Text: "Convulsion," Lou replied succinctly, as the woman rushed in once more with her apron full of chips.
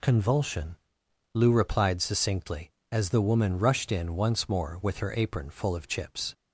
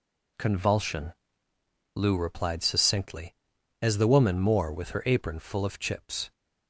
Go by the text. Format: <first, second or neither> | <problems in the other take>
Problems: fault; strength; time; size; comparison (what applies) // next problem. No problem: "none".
first | skips "rushed in once"; at 4.3 s